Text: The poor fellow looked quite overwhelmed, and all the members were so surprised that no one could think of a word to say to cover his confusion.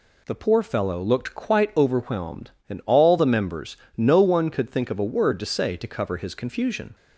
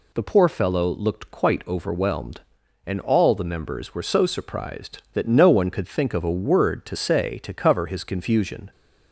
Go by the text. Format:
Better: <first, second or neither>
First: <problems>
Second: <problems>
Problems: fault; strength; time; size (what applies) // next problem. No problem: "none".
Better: second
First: skips "were so surprised that"; at 3.8 s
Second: none